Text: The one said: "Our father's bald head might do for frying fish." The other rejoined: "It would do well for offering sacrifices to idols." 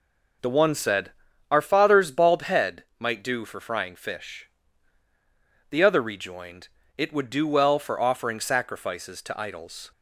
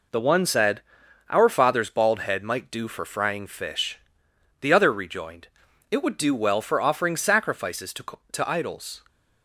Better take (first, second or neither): first